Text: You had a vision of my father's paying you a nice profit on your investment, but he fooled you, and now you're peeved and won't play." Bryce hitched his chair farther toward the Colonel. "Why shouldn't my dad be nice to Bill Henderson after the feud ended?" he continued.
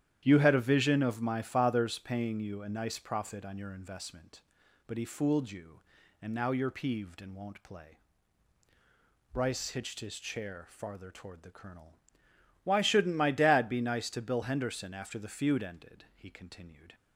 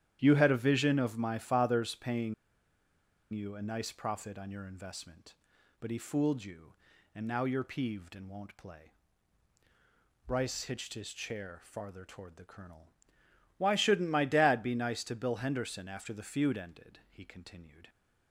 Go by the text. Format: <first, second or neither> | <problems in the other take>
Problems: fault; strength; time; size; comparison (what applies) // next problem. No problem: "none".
first | starts louder than the rest; strong; until 1.2 s; 10.5 dB; strong in the first // pauses between "paying" and "you"; at 2.3 s; 0.98 s long